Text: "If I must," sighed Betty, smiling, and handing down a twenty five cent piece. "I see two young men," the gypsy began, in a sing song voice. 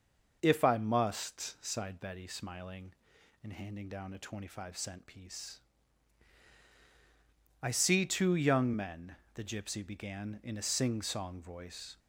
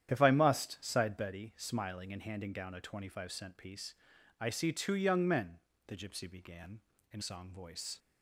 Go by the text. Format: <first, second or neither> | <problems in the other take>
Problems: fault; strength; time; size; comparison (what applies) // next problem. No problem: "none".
first | starts louder than the rest; strong; until 1.1 s; 10 dB // skips "a sing"; at 7.2 s